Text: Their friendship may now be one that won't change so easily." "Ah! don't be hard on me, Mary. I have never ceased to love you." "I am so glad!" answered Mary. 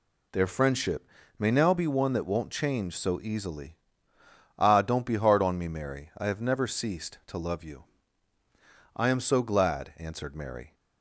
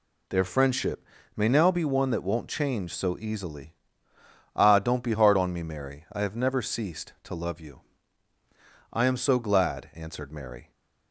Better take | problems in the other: neither | pauses between "friendship" and "may"; slight; the same in both

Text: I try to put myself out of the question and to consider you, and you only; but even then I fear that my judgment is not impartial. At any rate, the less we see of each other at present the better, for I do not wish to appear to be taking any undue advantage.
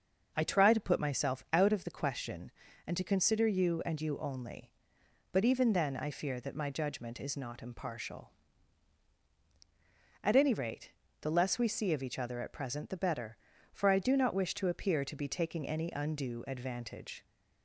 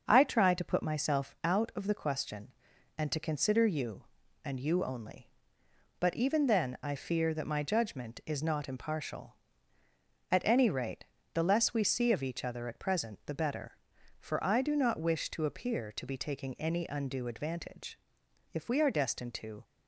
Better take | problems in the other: first | starts louder than the rest; until 1.0 s; 6.5 dB; noticeable in the first // goes on to say "If we are destined to"; noticeable; from 18.5 s on; 1.1 s long

